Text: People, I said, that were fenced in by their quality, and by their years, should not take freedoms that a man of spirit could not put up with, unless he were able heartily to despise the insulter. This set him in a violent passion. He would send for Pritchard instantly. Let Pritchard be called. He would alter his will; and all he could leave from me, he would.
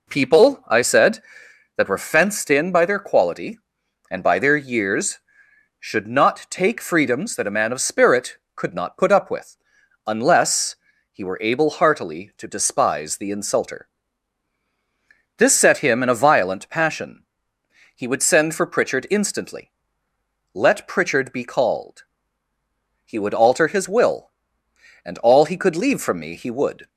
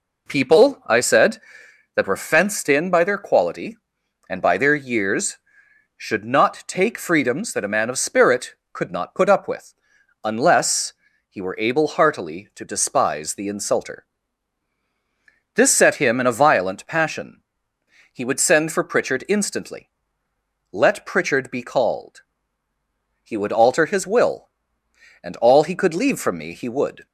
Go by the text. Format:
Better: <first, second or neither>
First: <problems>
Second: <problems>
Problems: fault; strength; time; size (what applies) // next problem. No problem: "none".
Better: neither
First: pauses between "unless" and "he"; slight; at 10.7 s; 0.34 s long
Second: pauses between "unless" and "he"; slight; at 10.9 s; 0.34 s long